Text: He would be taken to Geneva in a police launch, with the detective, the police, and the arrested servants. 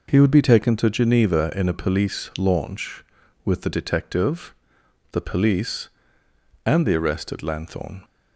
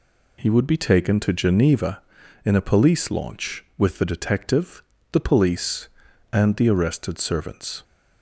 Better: second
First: says "lanthorn" for "servants"; at 7.4 s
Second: none

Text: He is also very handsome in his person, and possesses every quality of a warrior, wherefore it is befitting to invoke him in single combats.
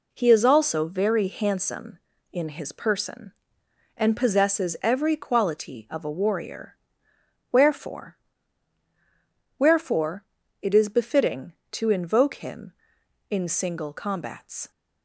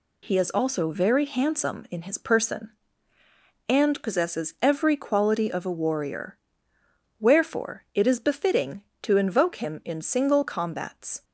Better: second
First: says "wherefore" twice; at 9.5 s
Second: none

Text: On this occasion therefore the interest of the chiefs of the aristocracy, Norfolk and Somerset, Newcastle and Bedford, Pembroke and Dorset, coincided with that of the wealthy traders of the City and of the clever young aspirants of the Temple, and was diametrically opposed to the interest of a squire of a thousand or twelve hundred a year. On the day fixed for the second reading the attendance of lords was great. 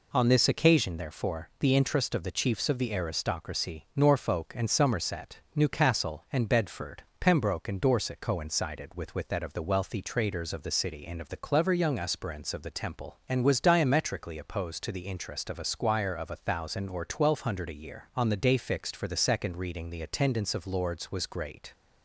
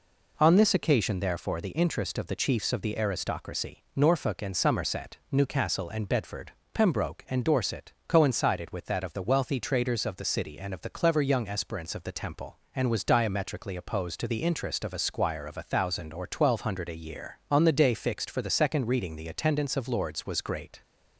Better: second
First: says "with" twice; at 9.1 s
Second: none

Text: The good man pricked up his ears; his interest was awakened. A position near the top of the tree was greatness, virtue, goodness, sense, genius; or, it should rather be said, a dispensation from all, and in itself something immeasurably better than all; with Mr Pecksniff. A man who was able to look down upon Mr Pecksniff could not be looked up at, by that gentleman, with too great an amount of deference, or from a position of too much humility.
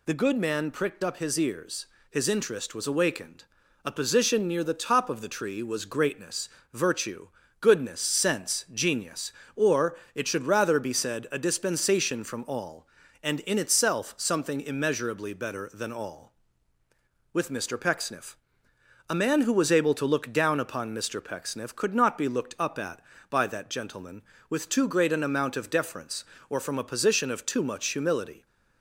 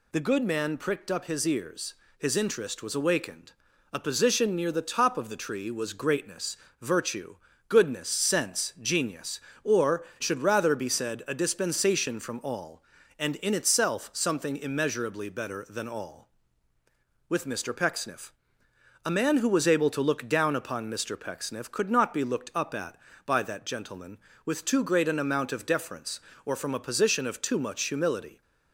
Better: first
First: none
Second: skips "it"; at 10.1 s

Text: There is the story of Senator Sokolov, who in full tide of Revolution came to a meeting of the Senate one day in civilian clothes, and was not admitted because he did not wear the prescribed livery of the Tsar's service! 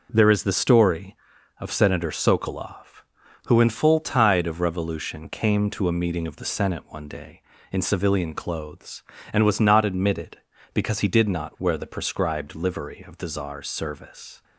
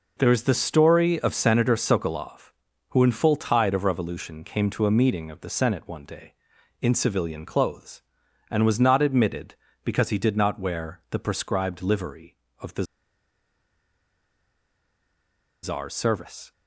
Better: first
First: none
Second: pauses between "the" and "Tsar's"; strong; at 12.8 s; 2.8 s long

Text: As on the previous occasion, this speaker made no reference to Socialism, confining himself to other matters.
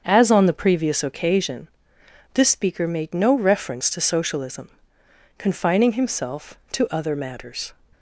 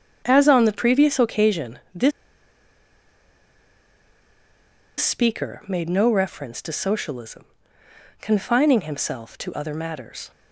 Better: first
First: starts louder than the rest; until 1.0 s; 7 dB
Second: starts louder than the rest; strong; until 1.2 s; 8 dB // pauses between "this" and "speaker"; strong; at 2.1 s; 2.8 s long

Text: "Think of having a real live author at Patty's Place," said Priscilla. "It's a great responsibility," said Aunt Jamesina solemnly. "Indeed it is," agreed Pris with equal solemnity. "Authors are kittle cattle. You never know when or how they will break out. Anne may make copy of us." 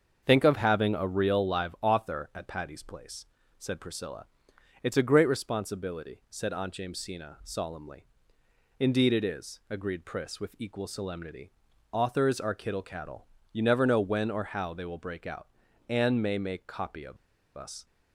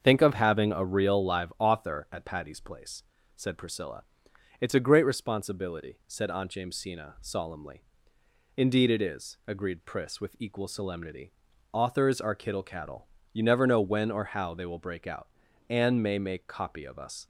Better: second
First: starts louder than the rest; until 1.2 s; 7 dB // pauses between "of" and "us"; at 17.1 s; 0.40 s long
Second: starts louder than the rest; until 1.0 s; 7 dB

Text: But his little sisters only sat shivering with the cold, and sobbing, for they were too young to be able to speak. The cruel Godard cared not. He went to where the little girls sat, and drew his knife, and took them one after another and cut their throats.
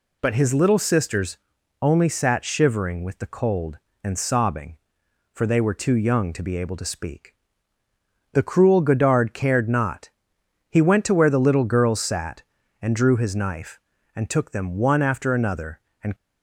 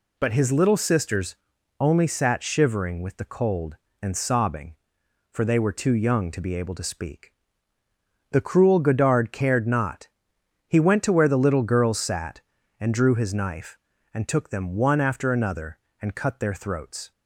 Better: second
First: pauses between "sisters" and "only"; at 1.3 s; 0.44 s long // stops before "cut their throats"; at 16.1 s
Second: pauses between "sisters" and "only"; at 1.3 s; 0.44 s long

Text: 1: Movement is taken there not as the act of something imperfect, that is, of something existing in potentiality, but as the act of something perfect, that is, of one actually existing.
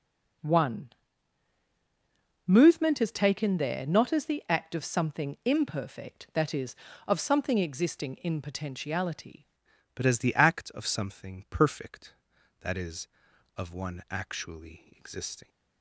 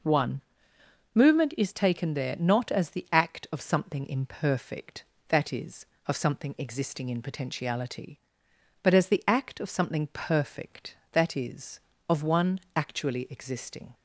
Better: second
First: changes voice at "but"; from 9.9 s on; 5.5 s long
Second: none

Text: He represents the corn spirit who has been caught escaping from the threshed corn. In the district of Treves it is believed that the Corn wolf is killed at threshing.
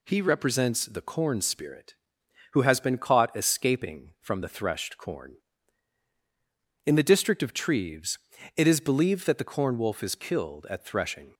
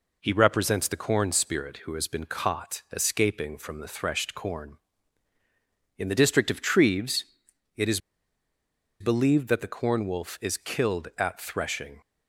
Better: first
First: pauses between "Treves" and "it"; at 8.1 s; 0.38 s long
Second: pauses between "Treves" and "it"; noticeable; at 7.2 s; 0.50 s long // pauses between "is" and "believed"; at 8.0 s; 1.0 s long

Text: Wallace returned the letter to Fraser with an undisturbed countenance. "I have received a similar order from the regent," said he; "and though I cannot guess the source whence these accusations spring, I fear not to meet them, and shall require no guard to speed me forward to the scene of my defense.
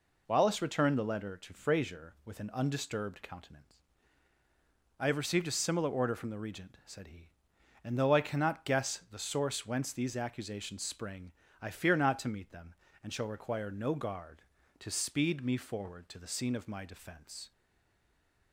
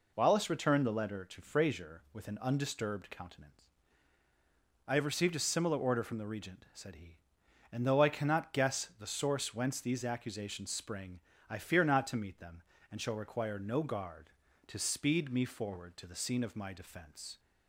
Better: second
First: stays silent after the last word; from 17.5 s on; 1.0 s long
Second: none

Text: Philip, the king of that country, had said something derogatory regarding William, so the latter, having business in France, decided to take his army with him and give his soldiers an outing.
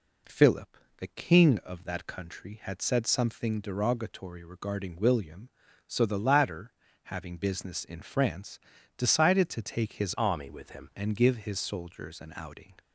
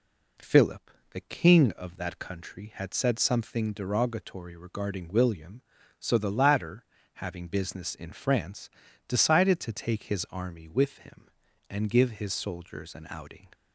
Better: second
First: changes voice from "army" to "him"; from 10.1 to 10.8 s; 0.7 s long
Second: none

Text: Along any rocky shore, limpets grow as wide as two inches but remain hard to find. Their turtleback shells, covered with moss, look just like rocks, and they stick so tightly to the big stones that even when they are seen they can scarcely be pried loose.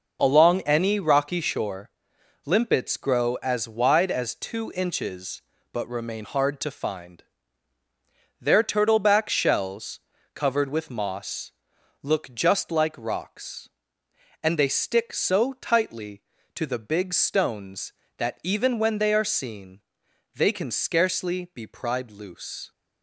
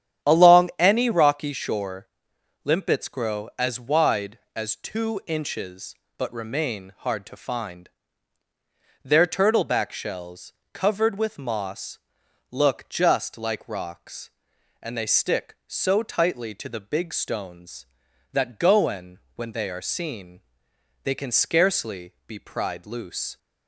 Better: first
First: pauses between "seen" and "they"; noticeable; at 19.7 s; 0.56 s long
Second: starts louder than the rest; strong; until 1.3 s; 9.5 dB // says "goen" for "even"; at 18.5 s // pauses between "seen" and "they"; noticeable; at 20.3 s; 0.64 s long // pauses between "scarcely" and "be"; slight; at 22.1 s; 0.16 s long

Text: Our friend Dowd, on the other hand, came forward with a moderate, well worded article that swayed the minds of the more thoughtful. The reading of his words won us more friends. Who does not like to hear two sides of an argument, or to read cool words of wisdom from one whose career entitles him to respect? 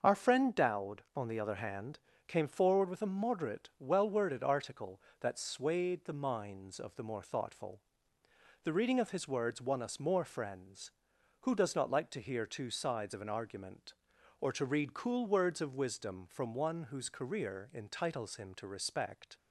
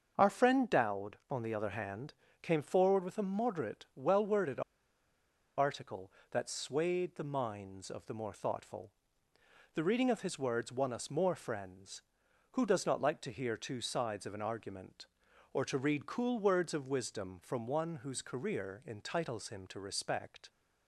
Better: first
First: starts louder than the rest; until 1.0 s; 6.5 dB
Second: starts louder than the rest; until 1.1 s; 6.5 dB // pauses between "worded" and "article"; noticeable; at 4.6 s; 0.96 s long

